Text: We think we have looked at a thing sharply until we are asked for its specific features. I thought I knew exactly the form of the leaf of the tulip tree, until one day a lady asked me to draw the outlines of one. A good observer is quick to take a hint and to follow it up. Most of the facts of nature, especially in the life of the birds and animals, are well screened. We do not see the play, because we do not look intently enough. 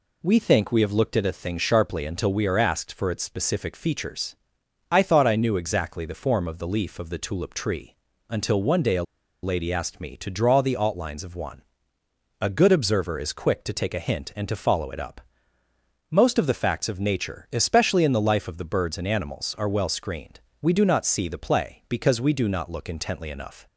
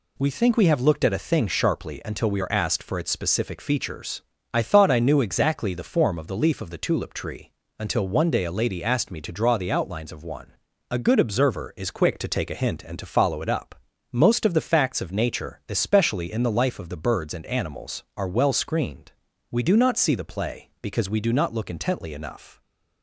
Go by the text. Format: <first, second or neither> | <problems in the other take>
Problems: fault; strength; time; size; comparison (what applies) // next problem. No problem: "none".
second | pauses between "a" and "lady"; at 9.0 s; 0.40 s long